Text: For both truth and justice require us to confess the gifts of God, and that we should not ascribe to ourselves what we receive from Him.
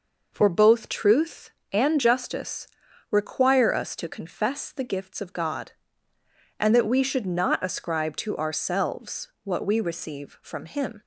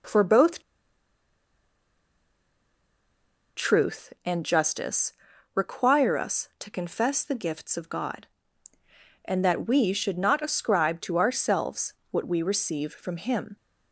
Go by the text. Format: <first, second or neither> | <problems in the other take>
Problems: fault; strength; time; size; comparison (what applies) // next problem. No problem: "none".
first | pauses between "both" and "truth"; strong; at 0.6 s; 2.9 s long // pauses between "justice" and "require"; at 5.1 s; 0.42 s long; also in the first // pauses between "ourselves" and "what"; slight; at 11.9 s; 0.18 s long; slight in the first